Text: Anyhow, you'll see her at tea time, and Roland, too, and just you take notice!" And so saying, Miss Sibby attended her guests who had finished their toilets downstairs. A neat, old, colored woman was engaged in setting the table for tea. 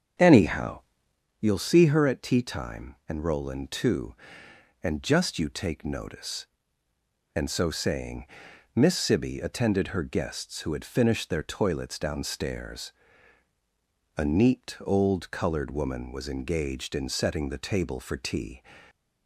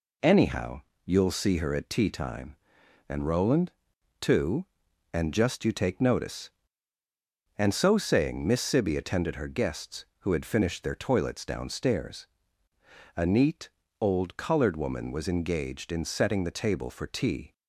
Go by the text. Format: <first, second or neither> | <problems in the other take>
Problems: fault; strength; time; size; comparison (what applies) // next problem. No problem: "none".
second | starts louder than the rest; strong; until 1.4 s; 8 dB